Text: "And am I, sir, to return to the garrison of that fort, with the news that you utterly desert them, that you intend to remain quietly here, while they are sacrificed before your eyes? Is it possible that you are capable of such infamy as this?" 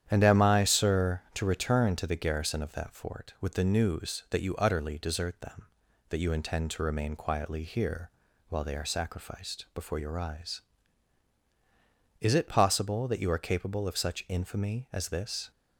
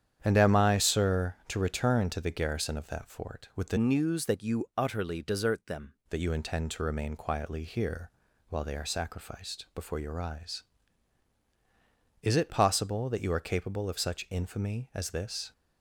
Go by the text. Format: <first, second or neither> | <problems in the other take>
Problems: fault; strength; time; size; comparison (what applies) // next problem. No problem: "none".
first | starts louder than the rest; strong; until 1.2 s; 9 dB; strong in the first // changes voice from "news" to "them"; from 3.7 to 5.9 s; 2.2 s long